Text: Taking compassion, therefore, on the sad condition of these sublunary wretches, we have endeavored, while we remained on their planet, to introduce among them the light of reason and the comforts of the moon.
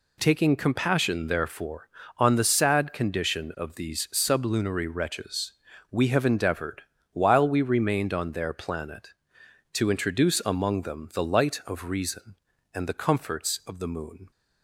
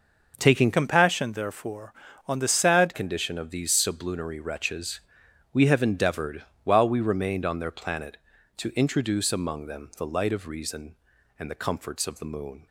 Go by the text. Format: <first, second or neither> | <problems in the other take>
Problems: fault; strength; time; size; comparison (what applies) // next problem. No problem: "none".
first | changes voice from "compassion" to "sad"; from 0.7 to 2.9 s; 2.2 s long